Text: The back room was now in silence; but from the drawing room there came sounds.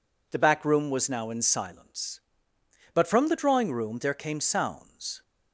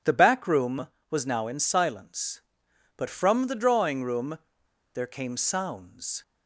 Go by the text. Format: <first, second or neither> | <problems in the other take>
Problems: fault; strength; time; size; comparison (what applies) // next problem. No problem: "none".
first | pauses between "room" and "there"; noticeable; at 4.3 s; 0.57 s long